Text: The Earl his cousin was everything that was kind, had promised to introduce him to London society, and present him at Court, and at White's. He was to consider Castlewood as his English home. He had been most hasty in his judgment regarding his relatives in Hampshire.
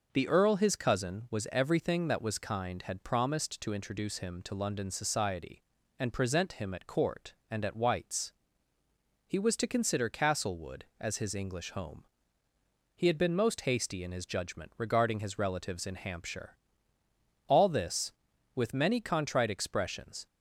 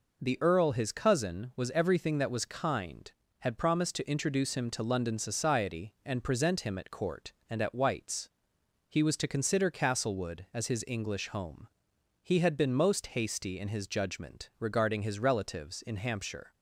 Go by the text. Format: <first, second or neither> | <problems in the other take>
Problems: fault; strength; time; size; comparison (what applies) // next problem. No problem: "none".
second | goes on to say "All this with many contrite expressions"; strong; from 17.4 s on; 2.8 s long